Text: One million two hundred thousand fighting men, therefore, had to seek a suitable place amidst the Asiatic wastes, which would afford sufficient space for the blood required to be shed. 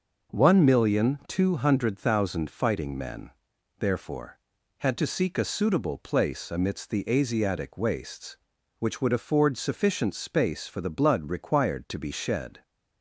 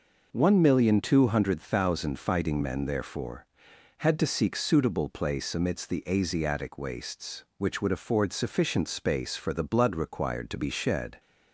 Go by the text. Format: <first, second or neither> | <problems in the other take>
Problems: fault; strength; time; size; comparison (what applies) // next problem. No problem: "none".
first | skips "a"; at 4.5 s